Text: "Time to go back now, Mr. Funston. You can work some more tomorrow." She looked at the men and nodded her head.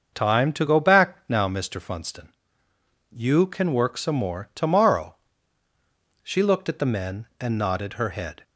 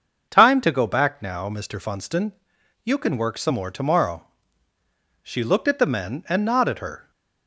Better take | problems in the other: first | starts louder than the rest; until 1.3 s; 6.5 dB; also in the first // stops before "head"; at 7.1 s

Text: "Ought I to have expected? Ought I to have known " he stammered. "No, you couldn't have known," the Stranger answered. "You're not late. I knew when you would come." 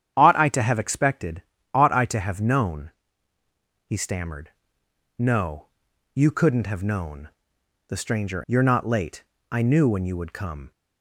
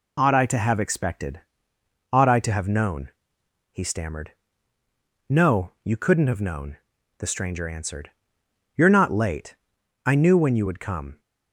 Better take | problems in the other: second | starts louder than the rest; strong; until 1.1 s; 9.5 dB // skips "answered"; at 8.4 s

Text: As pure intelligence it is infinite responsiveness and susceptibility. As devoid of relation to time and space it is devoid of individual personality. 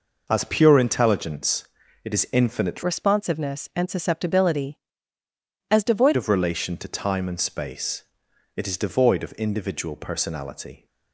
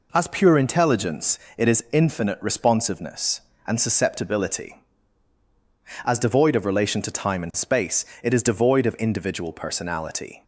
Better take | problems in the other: second | pauses between "intelligence" and "it"; at 1.6 s; 0.38 s long; slight in the second // changes voice from "responsiveness" to "devoid"; from 2.8 to 6.1 s; 3.3 s long // pauses between "space" and "it"; noticeable; at 8.0 s; 0.54 s long; slight in the second

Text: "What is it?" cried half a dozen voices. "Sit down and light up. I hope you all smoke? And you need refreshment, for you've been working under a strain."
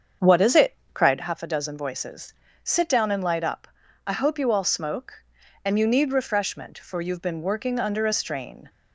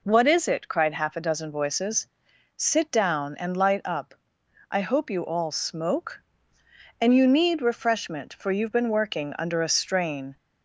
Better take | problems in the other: second | starts louder than the rest; strong; until 1.2 s; 7 dB

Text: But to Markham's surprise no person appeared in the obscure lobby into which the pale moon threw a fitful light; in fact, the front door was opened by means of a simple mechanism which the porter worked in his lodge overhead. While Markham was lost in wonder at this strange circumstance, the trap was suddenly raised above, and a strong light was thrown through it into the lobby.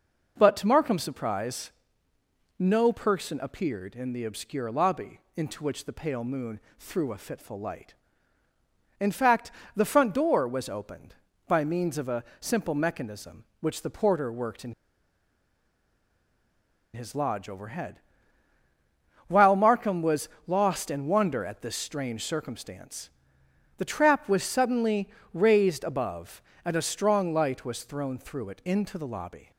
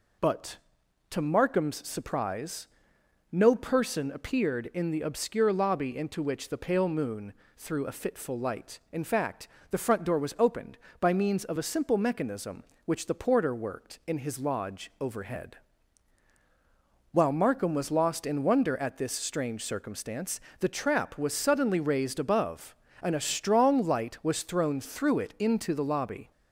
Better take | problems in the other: second | pauses between "surprise" and "no"; noticeable; at 1.7 s; 0.88 s long; noticeable in the second // pauses between "lobby" and "into"; slight; at 5.1 s; 0.16 s long // pauses between "moon" and "threw"; slight; at 6.5 s; 0.20 s long; slight in the second // pauses between "a" and "simple"; slight; at 12.2 s; 0.16 s long // pauses between "in" and "his"; strong; at 14.7 s; 2.2 s long // pauses between "was" and "lost"; slight; at 20.2 s; 0.18 s long // pauses between "suddenly" and "raised"; slight; at 25.1 s; 0.24 s long

